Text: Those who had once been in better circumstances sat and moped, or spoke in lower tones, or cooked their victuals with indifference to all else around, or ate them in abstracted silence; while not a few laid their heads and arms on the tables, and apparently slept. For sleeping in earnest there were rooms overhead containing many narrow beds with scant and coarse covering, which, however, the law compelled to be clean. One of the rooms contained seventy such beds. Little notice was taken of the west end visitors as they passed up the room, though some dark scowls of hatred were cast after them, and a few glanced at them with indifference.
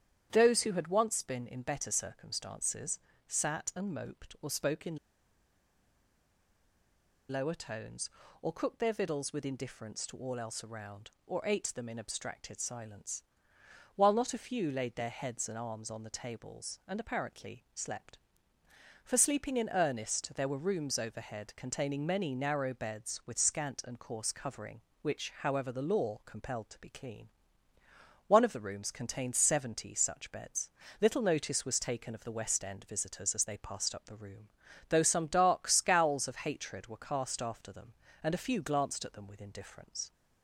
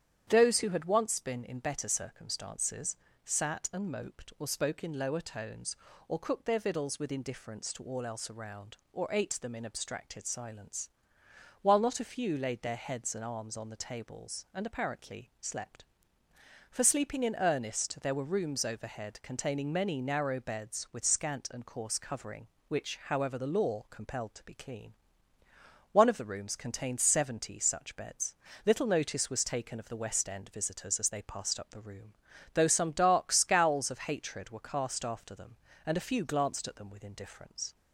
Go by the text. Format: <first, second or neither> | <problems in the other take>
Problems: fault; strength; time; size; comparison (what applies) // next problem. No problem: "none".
second | starts louder than the rest; strong; until 1.3 s; 9.5 dB; strong in the second // pauses between "circumstances" and "sat"; slight; at 2.9 s; 0.28 s long; slight in the second // pauses between "in" and "lower"; strong; at 4.9 s; 2.3 s long